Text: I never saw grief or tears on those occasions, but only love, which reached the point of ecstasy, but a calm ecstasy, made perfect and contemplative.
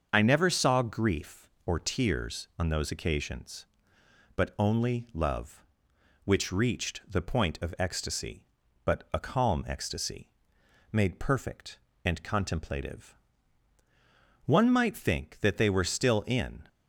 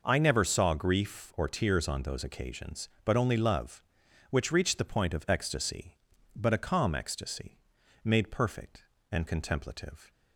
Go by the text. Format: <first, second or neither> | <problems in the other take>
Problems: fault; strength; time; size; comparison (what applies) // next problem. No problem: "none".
second | starts louder than the rest; until 1.1 s; 6.5 dB // goes on to say "One might think that they were still in"; strong; from 14.4 s on; 2.1 s long